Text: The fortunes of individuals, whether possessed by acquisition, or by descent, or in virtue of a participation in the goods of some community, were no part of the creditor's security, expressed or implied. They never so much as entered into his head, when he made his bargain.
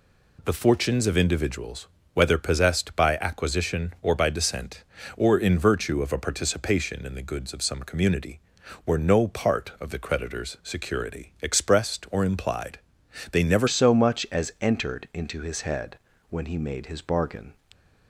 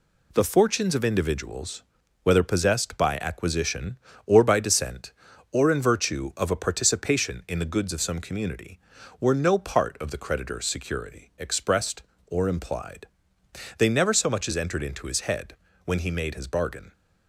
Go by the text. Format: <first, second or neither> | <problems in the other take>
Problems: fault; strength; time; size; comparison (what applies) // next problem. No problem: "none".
second | changes voice at "so"; from 13.6 s on; 3.9 s long